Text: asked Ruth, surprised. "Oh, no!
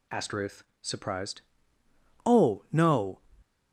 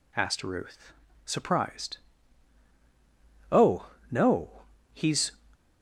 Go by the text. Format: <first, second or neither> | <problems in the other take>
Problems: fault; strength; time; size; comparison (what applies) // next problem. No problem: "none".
first | goes on to say "he's"; slight; from 4.9 s on; 0.38 s long